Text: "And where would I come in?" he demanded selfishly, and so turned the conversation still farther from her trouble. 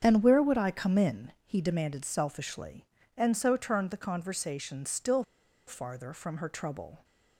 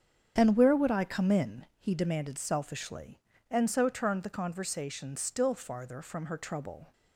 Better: second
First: starts louder than the rest; strong; until 1.0 s; 8 dB // pauses between "still" and "farther"; at 5.2 s; 0.43 s long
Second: starts louder than the rest; strong; until 1.3 s; 8 dB

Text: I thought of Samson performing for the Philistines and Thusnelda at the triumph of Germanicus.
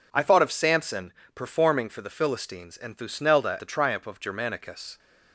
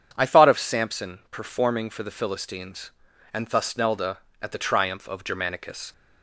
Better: second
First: pauses between "Samson" and "performing"; slight; at 1.1 s; 0.24 s long // skips "at"; at 3.5 s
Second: none

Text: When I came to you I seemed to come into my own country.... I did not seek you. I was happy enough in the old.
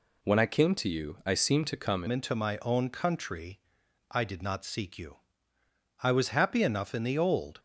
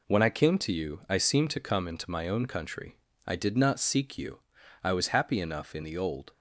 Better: second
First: changes voice at "into"; from 2.0 s on; 5.5 s long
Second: none

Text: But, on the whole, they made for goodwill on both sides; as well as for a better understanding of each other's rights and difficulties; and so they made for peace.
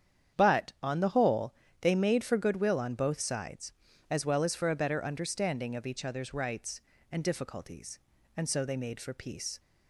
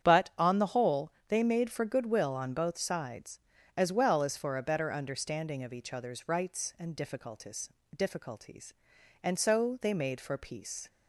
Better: first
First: starts louder than the rest; strong; until 1.4 s; 8.5 dB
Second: starts louder than the rest; strong; until 1.1 s; 9 dB // says "difficulties" twice; at 7.9 s

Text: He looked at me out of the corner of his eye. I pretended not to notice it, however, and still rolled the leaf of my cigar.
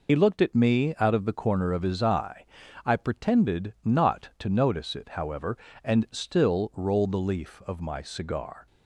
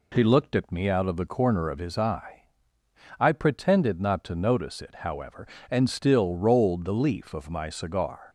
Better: second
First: loses the start of "He"; at 0.0 s; 55 ms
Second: none

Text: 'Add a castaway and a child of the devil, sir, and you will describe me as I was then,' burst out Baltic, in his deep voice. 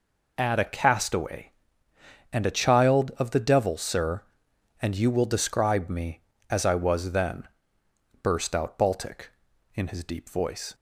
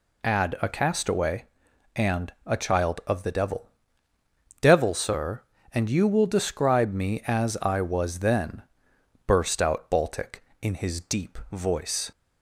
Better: first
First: none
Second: says "devil" twice; at 4.6 s

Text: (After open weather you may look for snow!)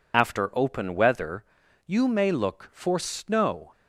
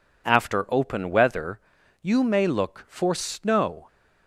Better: second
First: loses the start of "After"; at 0.1 s; 50 ms // pauses between "weather" and "you"; at 1.4 s; 0.42 s long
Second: pauses between "weather" and "you"; at 1.5 s; 0.42 s long

